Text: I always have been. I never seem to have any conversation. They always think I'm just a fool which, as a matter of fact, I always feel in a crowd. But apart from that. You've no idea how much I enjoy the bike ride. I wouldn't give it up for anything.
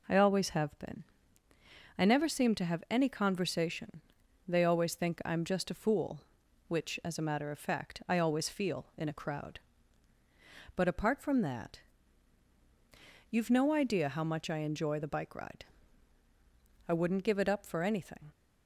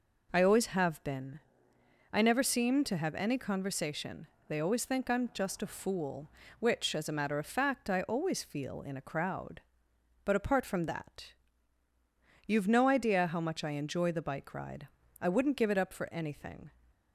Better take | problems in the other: neither | none

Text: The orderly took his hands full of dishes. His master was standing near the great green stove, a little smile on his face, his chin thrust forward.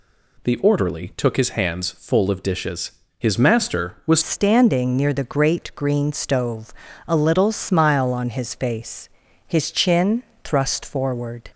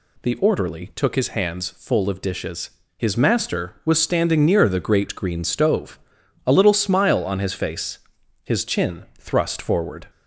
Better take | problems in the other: second | changes voice at "standing"; from 4.2 s on; 7.3 s long // pauses between "chin" and "thrust"; slight; at 10.2 s; 0.20 s long

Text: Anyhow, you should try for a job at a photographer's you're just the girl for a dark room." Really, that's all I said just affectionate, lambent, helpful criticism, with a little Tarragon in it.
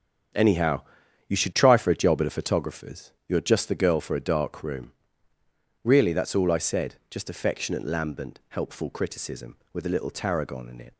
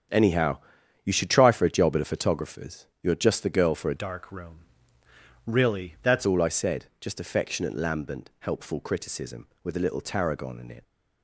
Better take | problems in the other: first | starts louder than the rest; strong; until 1.5 s; 8.5 dB; strong in the first // changes voice from "dark" to "that's"; from 3.9 to 6.2 s; 2.3 s long

